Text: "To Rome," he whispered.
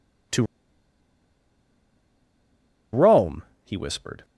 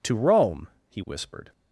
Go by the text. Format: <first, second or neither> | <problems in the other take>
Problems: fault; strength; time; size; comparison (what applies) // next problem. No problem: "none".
second | pauses between "To" and "Rome"; strong; at 0.4 s; 2.4 s long